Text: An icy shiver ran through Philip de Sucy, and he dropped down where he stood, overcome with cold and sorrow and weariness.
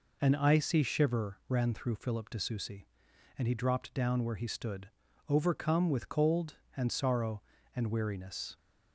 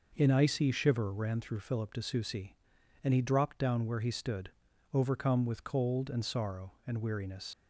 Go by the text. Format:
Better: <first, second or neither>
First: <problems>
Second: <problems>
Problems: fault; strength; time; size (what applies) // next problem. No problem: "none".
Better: first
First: none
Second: leaves "weariness" unfinished; at 7.5 s; 65 ms